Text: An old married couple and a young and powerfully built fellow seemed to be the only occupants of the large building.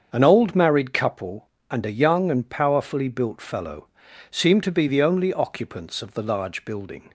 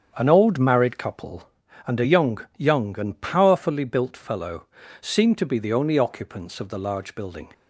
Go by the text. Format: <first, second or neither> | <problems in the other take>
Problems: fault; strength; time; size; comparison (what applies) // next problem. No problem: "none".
first | starts louder than the rest; strong; until 1.1 s; 7.5 dB; strong in the first // says "young" twice; at 2.5 s // pauses between "fellow" and "seemed"; slight; at 4.6 s; 0.34 s long; also in the first